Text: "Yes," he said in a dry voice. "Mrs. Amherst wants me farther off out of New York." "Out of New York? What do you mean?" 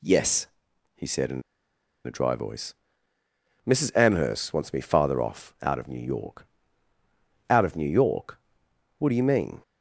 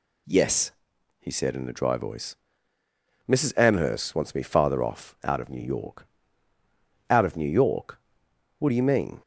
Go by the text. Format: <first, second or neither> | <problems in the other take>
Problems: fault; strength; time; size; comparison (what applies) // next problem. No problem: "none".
second | pauses between "in" and "a"; noticeable; at 1.4 s; 0.65 s long